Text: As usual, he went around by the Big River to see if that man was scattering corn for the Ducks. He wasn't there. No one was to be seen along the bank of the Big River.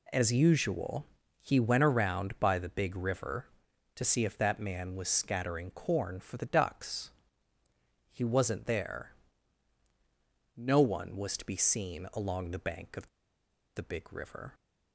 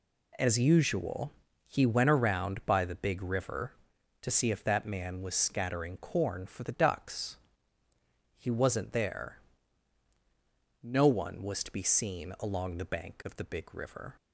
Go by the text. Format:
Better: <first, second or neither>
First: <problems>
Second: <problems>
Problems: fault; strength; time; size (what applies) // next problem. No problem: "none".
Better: second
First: pauses between "of" and "the"; noticeable; at 13.0 s; 0.68 s long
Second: none